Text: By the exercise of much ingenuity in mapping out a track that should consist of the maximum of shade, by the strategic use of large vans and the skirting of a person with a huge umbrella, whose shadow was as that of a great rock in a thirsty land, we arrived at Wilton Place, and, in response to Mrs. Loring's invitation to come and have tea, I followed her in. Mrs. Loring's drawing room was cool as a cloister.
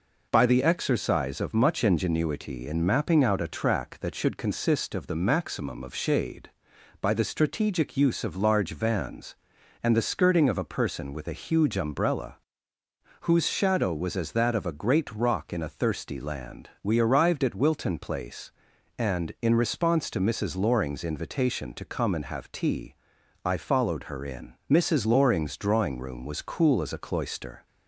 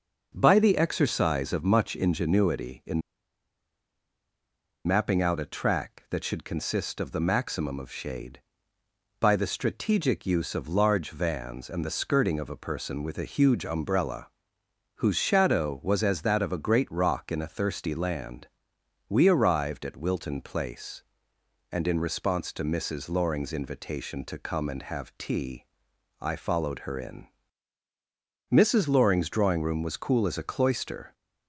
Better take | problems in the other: first | pauses between "in" and "mapping"; strong; at 3.0 s; 1.8 s long

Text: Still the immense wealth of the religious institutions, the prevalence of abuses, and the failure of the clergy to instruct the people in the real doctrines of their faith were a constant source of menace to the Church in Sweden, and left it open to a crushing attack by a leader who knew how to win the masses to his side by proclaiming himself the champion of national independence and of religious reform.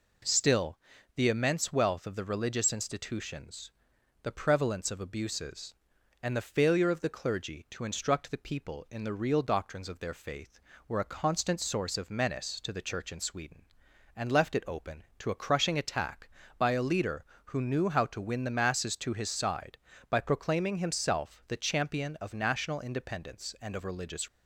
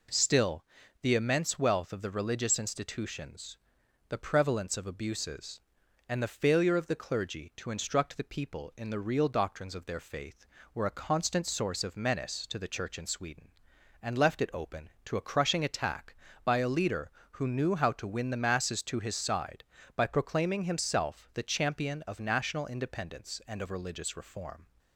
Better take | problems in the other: second | pauses between "Still" and "the"; at 0.7 s; 0.38 s long; also in the second // stops before "reform"; at 24.2 s

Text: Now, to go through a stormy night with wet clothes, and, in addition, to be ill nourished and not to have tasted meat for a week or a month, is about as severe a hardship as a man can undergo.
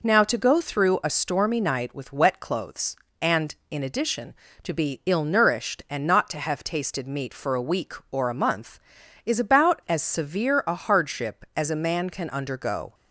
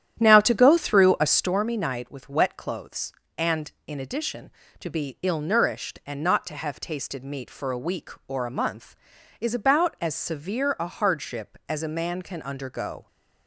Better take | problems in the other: first | starts louder than the rest; strong; until 1.5 s; 10.5 dB

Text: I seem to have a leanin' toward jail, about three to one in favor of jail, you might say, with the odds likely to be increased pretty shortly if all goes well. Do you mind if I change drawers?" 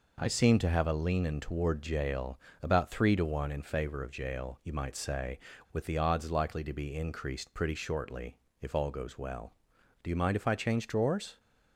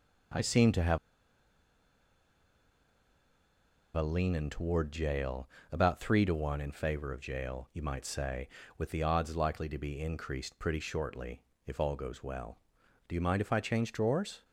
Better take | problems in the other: first | pauses between "have" and "a"; strong; at 0.9 s; 2.9 s long // pauses between "shortly" and "if"; slight; at 11.4 s; 0.24 s long; slight in the first

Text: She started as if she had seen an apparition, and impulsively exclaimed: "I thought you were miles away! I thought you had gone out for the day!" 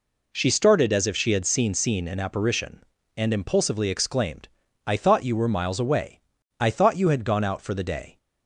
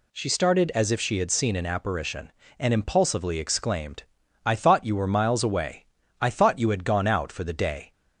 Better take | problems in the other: second | says "seen" twice; at 1.7 s

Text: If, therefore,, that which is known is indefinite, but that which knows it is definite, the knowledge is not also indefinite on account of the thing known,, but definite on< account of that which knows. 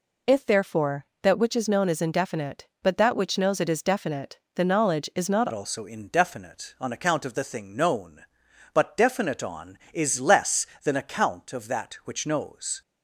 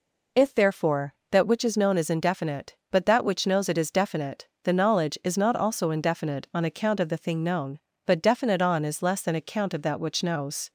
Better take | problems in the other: second | changes voice at "also"; from 5.5 s on; 7.3 s long

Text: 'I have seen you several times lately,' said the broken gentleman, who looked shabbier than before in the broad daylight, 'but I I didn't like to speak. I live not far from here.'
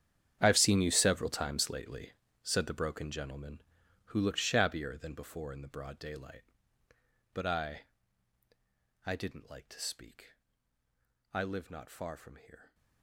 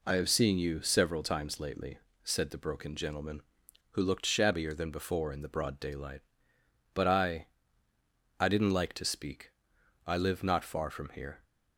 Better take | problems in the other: second | gets quieter; strong; throughout; 17 dB // pauses between "I" and "I"; at 7.8 s; 1.2 s long; noticeable in the second

